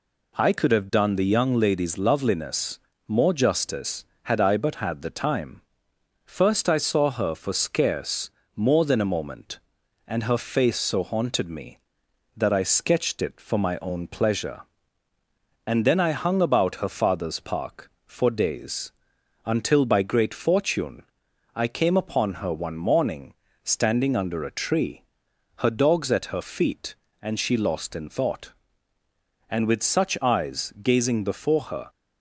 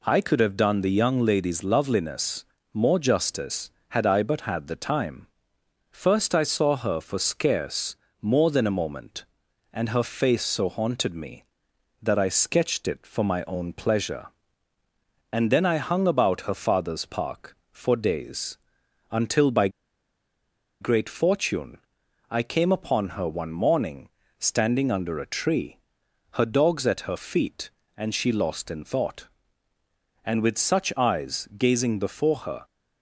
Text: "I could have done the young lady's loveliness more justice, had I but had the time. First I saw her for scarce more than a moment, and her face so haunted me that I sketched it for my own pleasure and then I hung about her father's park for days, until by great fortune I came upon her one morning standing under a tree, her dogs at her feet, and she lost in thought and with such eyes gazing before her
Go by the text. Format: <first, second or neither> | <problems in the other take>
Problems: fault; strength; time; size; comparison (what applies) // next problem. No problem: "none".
first | pauses between "loveliness" and "more"; slight; at 2.4 s; 0.30 s long; slight in the first // pauses between "scarce" and "more"; slight; at 7.9 s; 0.26 s long; slight in the first // pauses between "by" and "great"; at 19.6 s; 1.1 s long // pauses between "fortune" and "I"; noticeable; at 21.7 s; 0.54 s long; noticeable in the first // pauses between "morning" and "standing"; slight; at 24.0 s; 0.30 s long; slight in the first